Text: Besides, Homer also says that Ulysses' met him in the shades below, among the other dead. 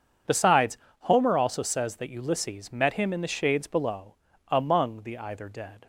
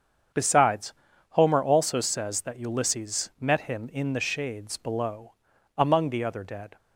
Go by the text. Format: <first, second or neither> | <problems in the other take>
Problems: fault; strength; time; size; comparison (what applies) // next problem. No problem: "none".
second | starts louder than the rest; strong; until 1.4 s; 7 dB; strong in the second // says "either" for "other"; at 5.1 s